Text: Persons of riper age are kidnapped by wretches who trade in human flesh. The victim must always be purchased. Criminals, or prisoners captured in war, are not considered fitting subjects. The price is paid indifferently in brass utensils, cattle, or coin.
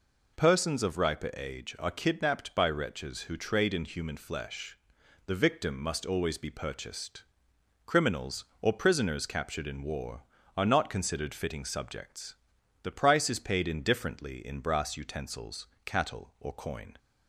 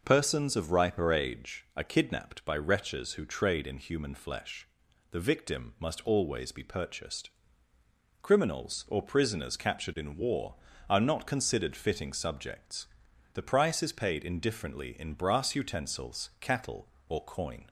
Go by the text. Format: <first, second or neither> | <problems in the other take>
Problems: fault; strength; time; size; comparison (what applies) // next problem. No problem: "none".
neither | none